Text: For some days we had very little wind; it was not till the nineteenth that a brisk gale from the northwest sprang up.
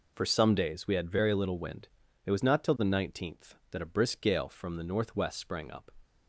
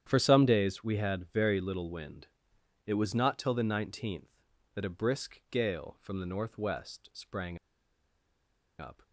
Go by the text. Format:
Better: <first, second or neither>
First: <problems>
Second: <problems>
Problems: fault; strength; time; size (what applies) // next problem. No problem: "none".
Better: first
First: none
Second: starts louder than the rest; strong; until 1.0 s; 9.5 dB // pauses between "sprang" and "up"; at 7.5 s; 1.2 s long